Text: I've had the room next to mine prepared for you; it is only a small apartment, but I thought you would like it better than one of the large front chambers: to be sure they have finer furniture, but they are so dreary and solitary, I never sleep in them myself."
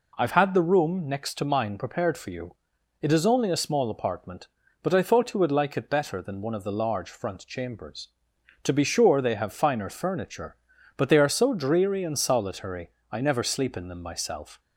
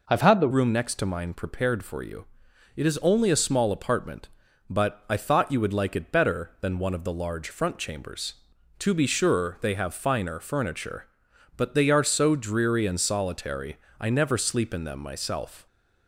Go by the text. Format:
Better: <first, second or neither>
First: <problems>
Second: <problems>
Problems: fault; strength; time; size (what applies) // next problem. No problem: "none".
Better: first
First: none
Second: changes voice at "room"; from 0.5 s on; 15.1 s long